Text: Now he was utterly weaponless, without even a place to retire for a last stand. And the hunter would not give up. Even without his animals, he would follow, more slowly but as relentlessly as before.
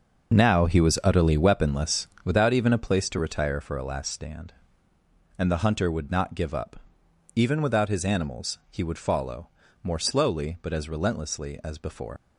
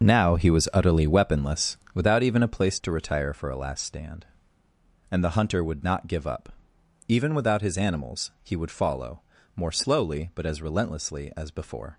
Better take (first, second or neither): second